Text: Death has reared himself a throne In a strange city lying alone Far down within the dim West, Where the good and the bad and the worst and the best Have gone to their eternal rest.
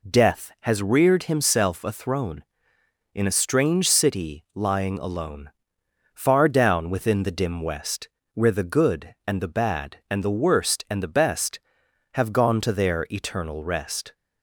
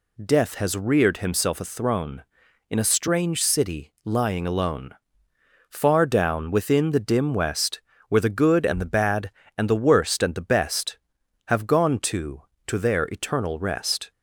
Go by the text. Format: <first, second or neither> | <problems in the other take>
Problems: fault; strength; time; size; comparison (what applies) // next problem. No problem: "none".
first | pauses between "alone" and "Far"; noticeable; at 4.9 s; 0.78 s long; noticeable in the first // says "to" twice; at 12.6 s